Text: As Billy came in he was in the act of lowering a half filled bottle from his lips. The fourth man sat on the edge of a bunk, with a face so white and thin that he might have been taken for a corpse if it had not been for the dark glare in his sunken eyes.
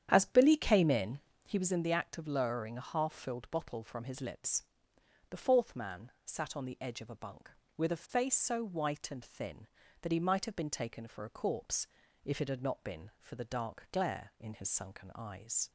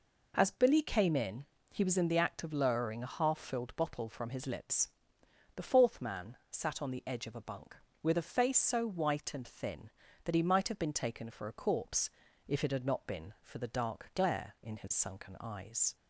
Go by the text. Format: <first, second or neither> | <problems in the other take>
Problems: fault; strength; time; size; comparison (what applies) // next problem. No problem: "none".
second | starts louder than the rest; strong; until 1.6 s; 9.5 dB // pauses between "in" and "he"; slight; at 1.1 s; 0.26 s long; slight in the second // pauses between "man" and "sat"; slight; at 6.0 s; 0.16 s long; slight in the second // pauses between "corpse" and "if"; at 11.8 s; 0.38 s long; also in the second